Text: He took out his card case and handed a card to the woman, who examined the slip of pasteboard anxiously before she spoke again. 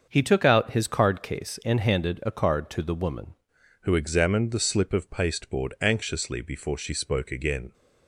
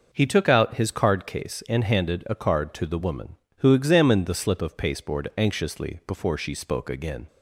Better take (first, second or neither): second